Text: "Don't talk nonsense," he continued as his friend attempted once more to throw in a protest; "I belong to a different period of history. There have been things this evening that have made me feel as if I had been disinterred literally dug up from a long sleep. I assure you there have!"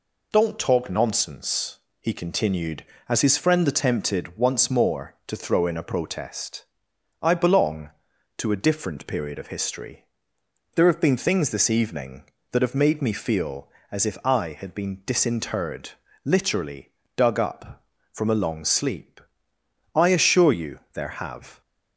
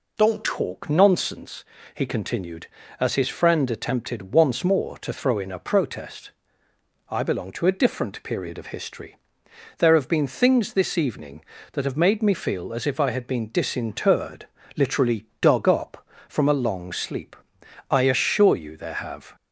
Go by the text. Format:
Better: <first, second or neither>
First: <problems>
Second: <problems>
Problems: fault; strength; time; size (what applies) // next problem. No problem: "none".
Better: first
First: pauses between "disinterred" and "literally"; slight; at 15.9 s; 0.34 s long // pauses between "literally" and "dug"; slight; at 16.9 s; 0.24 s long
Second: changes voice at "talk"; from 0.4 s on; 18.9 s long // pauses between "disinterred" and "literally"; slight; at 14.4 s; 0.32 s long // pauses between "literally" and "dug"; slight; at 15.2 s; 0.16 s long